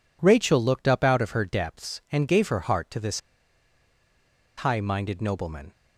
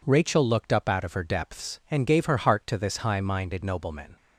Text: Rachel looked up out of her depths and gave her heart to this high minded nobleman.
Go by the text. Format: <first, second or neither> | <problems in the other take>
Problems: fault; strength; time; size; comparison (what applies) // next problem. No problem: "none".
second | pauses between "this" and "high"; strong; at 3.1 s; 1.3 s long